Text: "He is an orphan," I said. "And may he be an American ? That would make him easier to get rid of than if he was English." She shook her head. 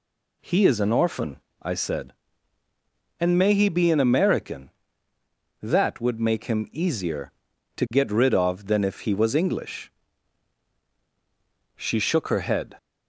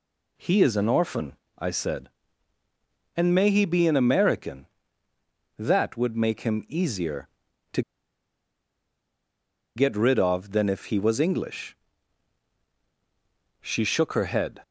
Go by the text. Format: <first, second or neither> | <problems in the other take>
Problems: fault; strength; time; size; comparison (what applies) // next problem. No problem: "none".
first | pauses between "to" and "get"; strong; at 7.8 s; 1.9 s long